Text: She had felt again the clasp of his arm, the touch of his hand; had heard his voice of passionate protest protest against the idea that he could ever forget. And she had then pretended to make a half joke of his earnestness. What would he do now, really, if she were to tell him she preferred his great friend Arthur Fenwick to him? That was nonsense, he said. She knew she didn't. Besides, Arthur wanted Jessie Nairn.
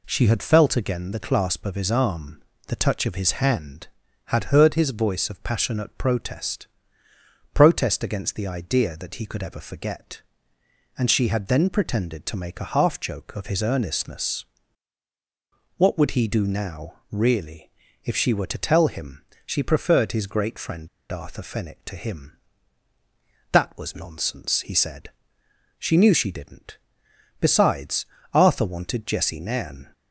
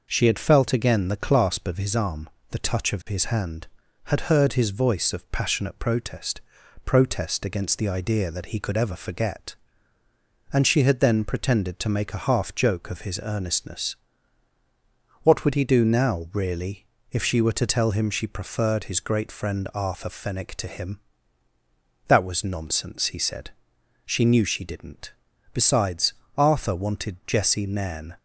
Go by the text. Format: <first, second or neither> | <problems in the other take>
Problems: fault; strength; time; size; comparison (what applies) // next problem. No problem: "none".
second | pauses between "protest" and "protest"; noticeable; at 6.6 s; 0.86 s long; also in the second // pauses between "him" and "she"; slight; at 19.2 s; 0.22 s long // pauses between "friend" and "Arthur"; slight; at 20.8 s; 0.24 s long